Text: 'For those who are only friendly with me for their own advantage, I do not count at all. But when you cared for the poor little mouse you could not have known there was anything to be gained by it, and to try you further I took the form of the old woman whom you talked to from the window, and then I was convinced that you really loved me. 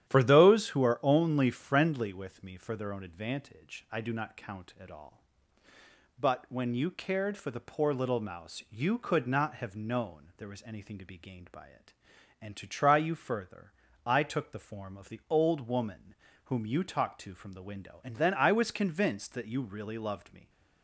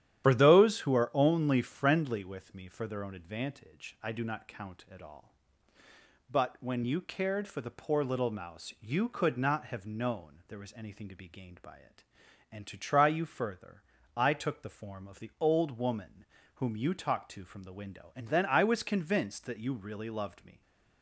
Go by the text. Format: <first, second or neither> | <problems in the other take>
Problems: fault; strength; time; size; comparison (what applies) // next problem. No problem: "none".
first | loses the start of "For"; at 0.2 s; 45 ms // starts louder than the rest; strong; until 1.2 s; 11 dB; strong in the first // pauses between "further" and "I"; slight; at 13.8 s; 0.32 s long; slight in the first // pauses between "woman" and "whom"; slight; at 16.2 s; 0.30 s long; slight in the first